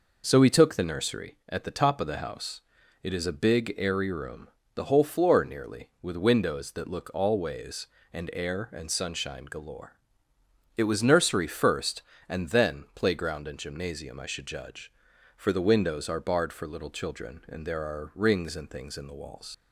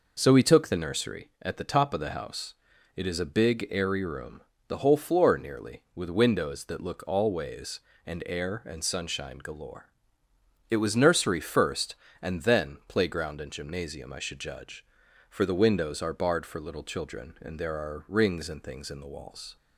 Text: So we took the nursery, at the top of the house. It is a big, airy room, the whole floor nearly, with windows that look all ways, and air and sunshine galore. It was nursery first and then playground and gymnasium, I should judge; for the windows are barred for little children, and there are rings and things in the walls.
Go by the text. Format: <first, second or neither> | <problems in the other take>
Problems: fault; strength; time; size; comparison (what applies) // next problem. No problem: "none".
second | leaves "walls" unfinished; at 19.5 s; 80 ms